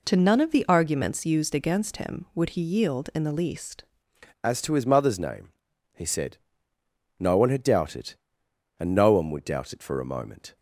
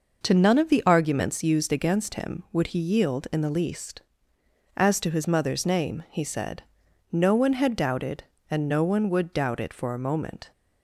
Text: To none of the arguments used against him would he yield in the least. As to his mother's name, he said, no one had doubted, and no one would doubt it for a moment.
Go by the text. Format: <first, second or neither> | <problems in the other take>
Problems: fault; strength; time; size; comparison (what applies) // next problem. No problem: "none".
second | changes voice at "As"; from 4.4 s on; 6.1 s long